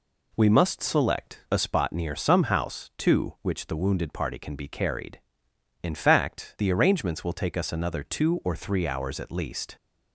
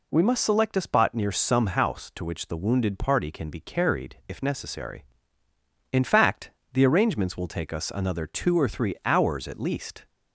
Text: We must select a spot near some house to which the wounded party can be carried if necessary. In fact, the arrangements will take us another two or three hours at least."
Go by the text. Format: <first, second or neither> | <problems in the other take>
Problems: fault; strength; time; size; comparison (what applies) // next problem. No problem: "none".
second | skips "if necessary"; at 5.5 s